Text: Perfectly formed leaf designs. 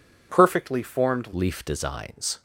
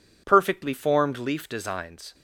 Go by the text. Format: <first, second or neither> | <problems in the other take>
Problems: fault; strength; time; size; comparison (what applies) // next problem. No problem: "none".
second | changes voice at "leaf"; from 1.3 s on; 1.1 s long